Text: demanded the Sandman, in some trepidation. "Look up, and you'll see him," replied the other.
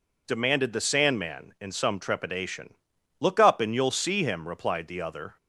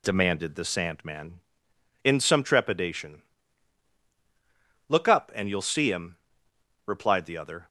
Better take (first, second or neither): neither